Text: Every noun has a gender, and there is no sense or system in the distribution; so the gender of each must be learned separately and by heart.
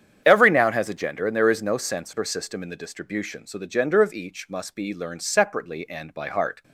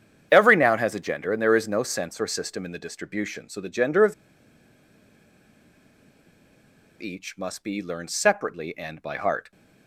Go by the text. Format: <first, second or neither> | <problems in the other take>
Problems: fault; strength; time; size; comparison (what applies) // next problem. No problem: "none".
first | starts louder than the rest; strong; until 1.3 s; 8.5 dB; strong in the first // pauses between "of" and "each"; strong; at 4.1 s; 2.8 s long